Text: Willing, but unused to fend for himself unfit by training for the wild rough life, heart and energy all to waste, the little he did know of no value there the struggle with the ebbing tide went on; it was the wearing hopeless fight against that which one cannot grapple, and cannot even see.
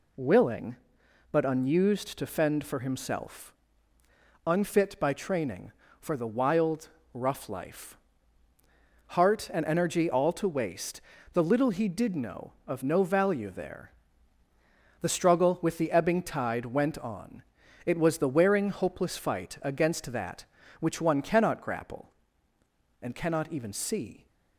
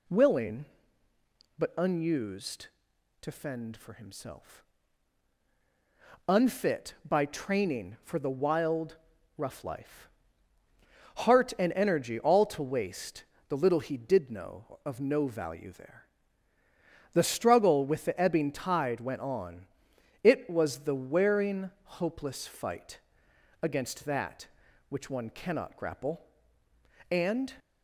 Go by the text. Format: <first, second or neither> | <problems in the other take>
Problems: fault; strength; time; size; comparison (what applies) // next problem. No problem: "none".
first | pauses between "himself" and "unfit"; strong; at 4.6 s; 1.6 s long; noticeable in the first // pauses between "wild" and "rough"; at 8.9 s; 0.40 s long; slight in the first // pauses between "there" and "the"; at 16.0 s; 1.0 s long; also in the first // pauses between "fight" and "against"; noticeable; at 23.0 s; 0.60 s long // stops before "cannot even see"; at 27.5 s